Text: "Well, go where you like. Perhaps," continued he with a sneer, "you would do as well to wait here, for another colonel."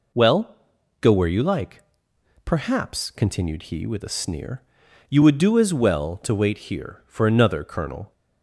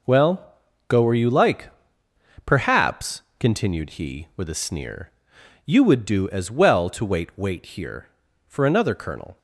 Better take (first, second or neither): first